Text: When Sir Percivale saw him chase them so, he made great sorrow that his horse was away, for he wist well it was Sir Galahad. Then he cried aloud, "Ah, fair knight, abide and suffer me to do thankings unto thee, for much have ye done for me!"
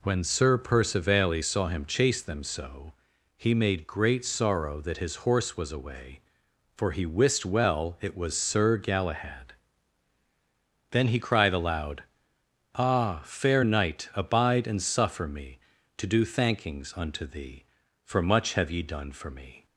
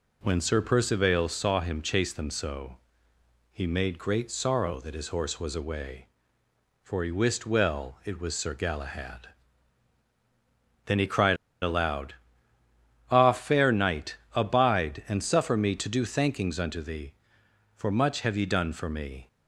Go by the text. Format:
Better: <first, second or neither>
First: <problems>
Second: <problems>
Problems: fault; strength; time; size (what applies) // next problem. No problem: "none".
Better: first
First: none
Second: pauses between "cried" and "aloud"; slight; at 11.3 s; 0.26 s long